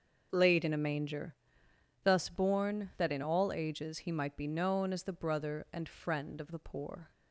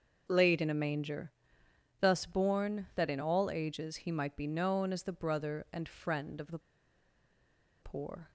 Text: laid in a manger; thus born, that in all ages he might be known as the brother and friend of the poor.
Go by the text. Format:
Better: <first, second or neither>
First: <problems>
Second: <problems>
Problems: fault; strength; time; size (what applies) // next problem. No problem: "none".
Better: first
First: starts louder than the rest; until 1.3 s; 6.5 dB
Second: starts louder than the rest; until 1.2 s; 6.5 dB // pauses between "the" and "poor"; at 6.5 s; 1.2 s long